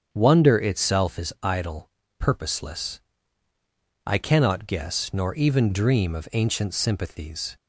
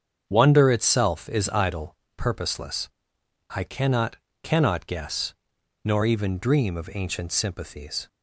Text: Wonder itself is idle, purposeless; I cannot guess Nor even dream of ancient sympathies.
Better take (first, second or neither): first